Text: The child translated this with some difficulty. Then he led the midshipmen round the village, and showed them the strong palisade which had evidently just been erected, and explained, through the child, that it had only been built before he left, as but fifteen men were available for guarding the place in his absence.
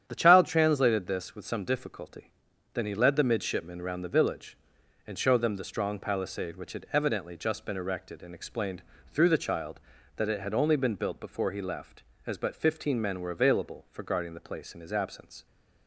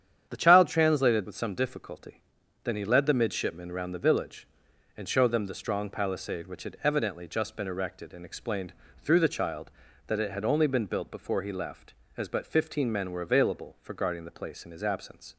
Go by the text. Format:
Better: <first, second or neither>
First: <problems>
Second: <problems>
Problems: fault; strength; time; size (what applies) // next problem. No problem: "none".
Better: first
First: starts louder than the rest; strong; until 1.0 s; 9 dB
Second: starts louder than the rest; strong; until 1.3 s; 9 dB // skips "this"; at 1.2 s